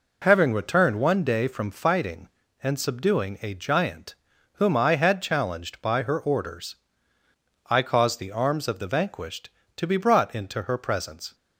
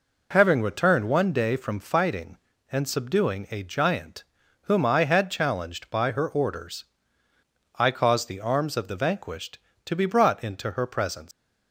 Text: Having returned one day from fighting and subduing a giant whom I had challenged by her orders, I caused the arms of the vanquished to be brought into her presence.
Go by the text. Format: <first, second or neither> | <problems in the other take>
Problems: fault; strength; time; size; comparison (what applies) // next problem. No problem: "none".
first | pauses between "giant" and "whom"; at 4.2 s; 0.38 s long; also in the first // leaves "presence" unfinished; at 11.3 s; 125 ms